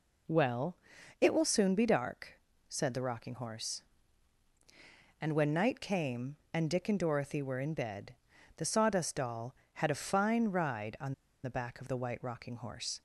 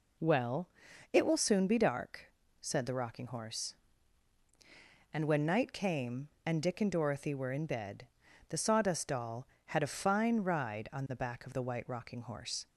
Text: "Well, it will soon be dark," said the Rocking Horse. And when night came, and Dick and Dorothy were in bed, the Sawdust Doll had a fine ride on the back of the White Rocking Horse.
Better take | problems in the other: second | pauses between "on" and "the"; slight; at 11.1 s; 0.29 s long

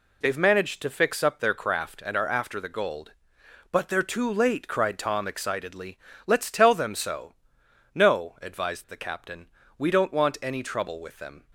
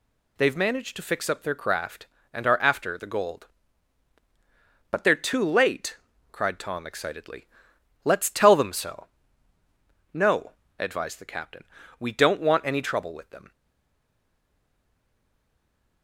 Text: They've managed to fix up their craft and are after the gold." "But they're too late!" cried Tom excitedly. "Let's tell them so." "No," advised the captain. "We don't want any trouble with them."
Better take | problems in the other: first | stays silent after the last word; strong; from 13.5 s on; 2.5 s long

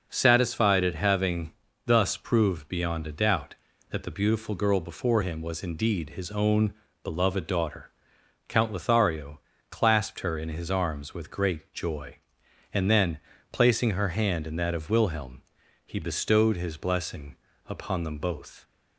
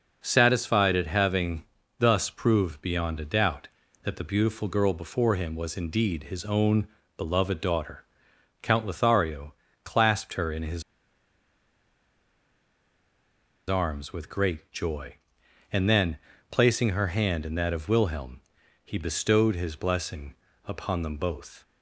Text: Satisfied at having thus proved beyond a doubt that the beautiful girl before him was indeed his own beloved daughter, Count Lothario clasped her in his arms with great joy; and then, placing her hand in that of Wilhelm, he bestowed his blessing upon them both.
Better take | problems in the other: first | pauses between "having" and "thus"; slight; at 1.6 s; 0.34 s long; slight in the first // pauses between "own" and "beloved"; slight; at 6.8 s; 0.30 s long; slight in the first // pauses between "Lothario" and "clasped"; slight; at 9.5 s; 0.30 s long; slight in the first // pauses between "his" and "arms"; strong; at 10.8 s; 2.8 s long // pauses between "blessing" and "upon"; slight; at 20.3 s; 0.30 s long; slight in the first

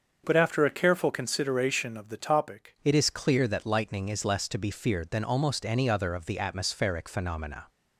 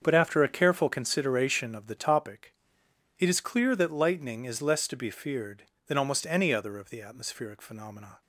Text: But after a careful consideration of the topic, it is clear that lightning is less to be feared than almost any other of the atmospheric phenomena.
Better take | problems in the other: second | starts louder than the rest; until 1.2 s; 6.5 dB; also in the second // changes voice at "it"; from 2.8 s on; 4.8 s long

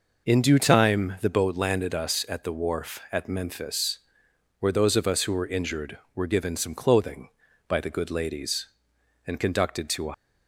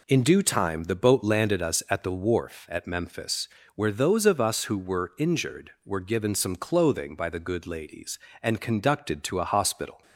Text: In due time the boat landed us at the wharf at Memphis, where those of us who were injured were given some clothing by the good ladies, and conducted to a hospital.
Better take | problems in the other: second | stops before "hospital"; at 10.1 s

